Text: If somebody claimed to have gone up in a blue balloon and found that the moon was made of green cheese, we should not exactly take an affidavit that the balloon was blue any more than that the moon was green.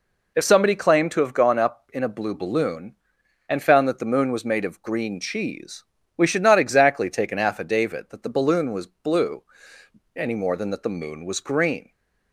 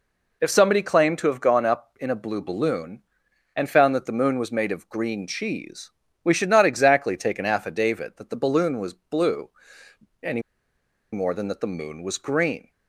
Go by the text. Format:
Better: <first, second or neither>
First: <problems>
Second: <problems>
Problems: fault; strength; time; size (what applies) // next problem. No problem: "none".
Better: first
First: pauses between "blue" and "any"; noticeable; at 9.4 s; 0.74 s long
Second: pauses between "blue" and "any"; noticeable; at 9.4 s; 0.74 s long // pauses between "any" and "more"; noticeable; at 10.4 s; 0.71 s long